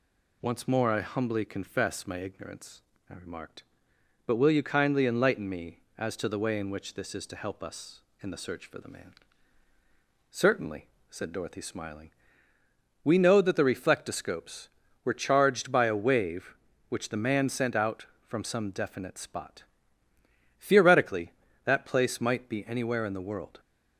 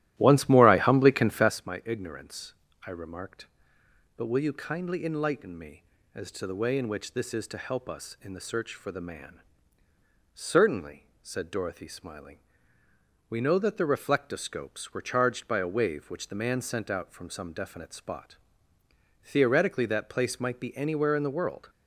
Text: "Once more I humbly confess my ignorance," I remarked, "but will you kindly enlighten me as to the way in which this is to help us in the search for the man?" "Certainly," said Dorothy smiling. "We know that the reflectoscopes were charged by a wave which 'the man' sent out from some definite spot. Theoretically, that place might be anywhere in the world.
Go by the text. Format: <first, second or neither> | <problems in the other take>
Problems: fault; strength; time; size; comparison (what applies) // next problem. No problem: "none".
first | starts louder than the rest; strong; until 1.6 s; 13 dB